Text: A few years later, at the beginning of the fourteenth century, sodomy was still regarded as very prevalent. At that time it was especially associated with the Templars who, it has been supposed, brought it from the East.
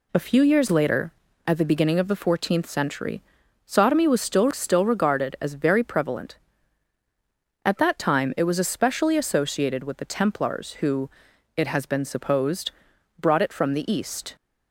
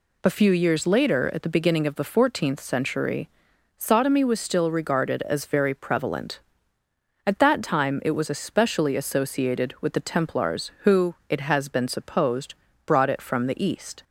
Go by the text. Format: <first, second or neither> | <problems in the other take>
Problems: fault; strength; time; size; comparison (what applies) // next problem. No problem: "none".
second | says "still" twice; at 4.4 s